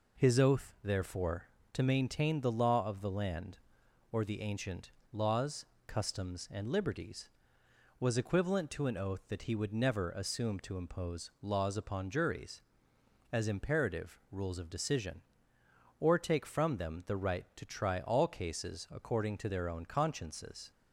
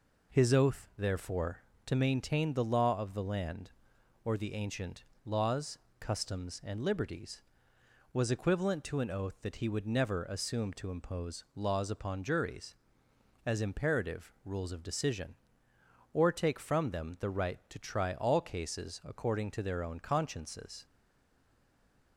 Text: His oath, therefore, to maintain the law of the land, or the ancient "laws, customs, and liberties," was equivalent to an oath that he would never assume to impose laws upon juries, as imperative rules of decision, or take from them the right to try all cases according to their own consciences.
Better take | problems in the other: first | pauses between "ancient" and "laws"; slight; at 5.0 s; 0.22 s long; slight in the first // stays silent after the last word; noticeable; from 20.8 s on; 1.3 s long

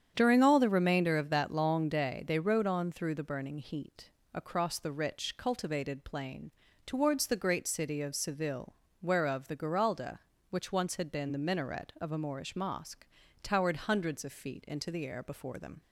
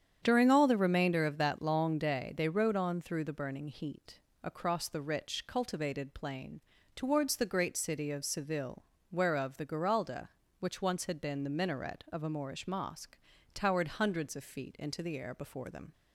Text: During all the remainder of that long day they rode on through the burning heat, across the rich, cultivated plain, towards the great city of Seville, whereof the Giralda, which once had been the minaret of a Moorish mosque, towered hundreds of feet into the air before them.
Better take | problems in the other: neither | starts louder than the rest; strong; the same in both

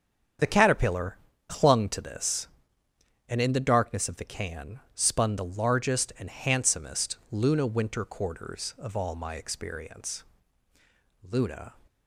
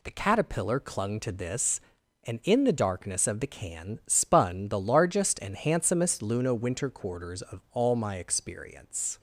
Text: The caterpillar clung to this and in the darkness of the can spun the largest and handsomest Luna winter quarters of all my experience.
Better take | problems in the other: second | starts louder than the rest; strong; until 1.7 s; 8 dB // pauses between "caterpillar" and "clung"; slight; at 1.1 s; 0.30 s long // goes on to say "Luna"; slight; from 11.3 s on; 0.44 s long

